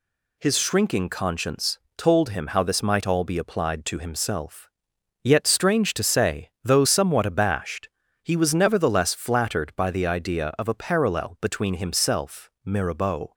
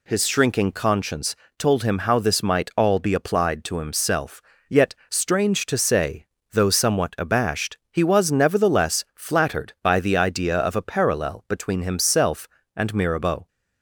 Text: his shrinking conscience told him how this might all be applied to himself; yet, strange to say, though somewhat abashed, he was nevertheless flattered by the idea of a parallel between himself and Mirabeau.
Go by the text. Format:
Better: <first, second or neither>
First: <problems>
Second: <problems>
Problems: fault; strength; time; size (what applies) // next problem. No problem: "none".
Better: second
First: pauses between "conscience" and "told"; slight; at 1.7 s; 0.18 s long // skips "and"; at 12.5 s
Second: pauses between "conscience" and "told"; slight; at 1.3 s; 0.24 s long